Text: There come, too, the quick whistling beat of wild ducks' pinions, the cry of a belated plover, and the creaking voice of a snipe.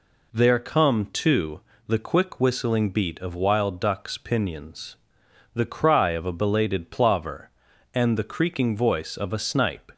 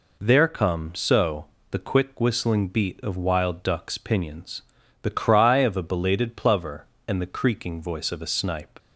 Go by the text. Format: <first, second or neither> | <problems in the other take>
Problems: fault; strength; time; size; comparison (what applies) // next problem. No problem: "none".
first | says "so" for "too"; at 0.9 s